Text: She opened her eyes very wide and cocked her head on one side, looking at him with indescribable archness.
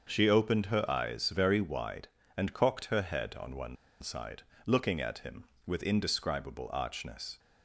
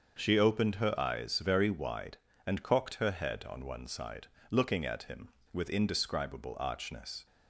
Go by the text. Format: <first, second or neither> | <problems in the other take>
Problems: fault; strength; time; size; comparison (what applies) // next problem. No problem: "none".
second | starts louder than the rest; until 1.0 s; 6.5 dB; also in the second // pauses between "one" and "side"; slight; at 3.7 s; 0.25 s long